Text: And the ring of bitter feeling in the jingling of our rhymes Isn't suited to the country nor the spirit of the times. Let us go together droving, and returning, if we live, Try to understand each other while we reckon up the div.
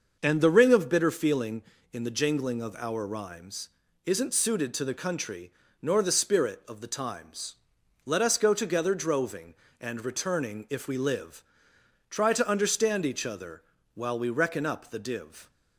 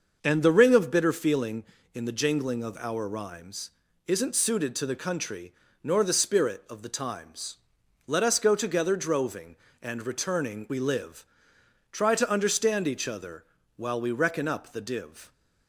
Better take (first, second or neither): first